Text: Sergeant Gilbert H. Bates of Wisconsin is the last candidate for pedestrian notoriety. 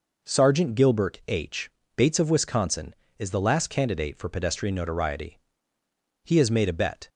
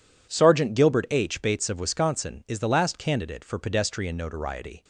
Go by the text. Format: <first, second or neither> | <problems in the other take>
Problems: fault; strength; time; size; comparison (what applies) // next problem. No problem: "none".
second | goes on to say "He has made a bet"; noticeable; from 6.2 s on; 0.84 s long